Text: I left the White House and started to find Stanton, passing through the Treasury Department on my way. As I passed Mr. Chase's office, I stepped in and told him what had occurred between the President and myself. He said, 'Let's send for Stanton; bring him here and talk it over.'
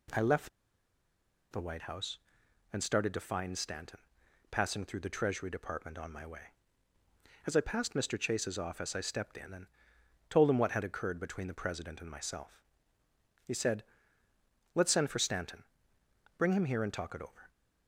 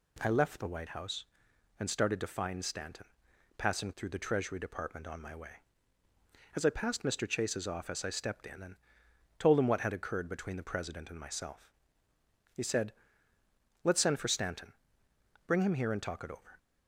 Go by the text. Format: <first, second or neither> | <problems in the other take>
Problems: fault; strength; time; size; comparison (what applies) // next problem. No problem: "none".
second | pauses between "left" and "the"; at 0.4 s; 1.0 s long // pauses between "and" and "told"; noticeable; at 9.6 s; 0.62 s long; noticeable in the second